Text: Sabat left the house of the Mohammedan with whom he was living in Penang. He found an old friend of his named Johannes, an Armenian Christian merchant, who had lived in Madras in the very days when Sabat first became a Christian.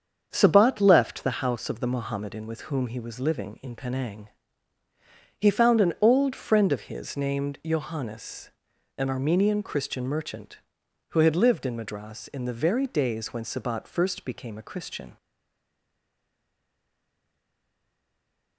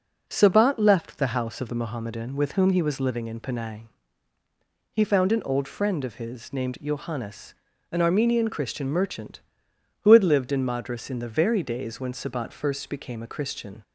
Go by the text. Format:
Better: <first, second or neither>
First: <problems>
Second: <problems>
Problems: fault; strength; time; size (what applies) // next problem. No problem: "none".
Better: second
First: starts louder than the rest; strong; until 1.3 s; 7.5 dB // stays silent after the last word; strong; from 15.1 s on; 3.4 s long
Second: none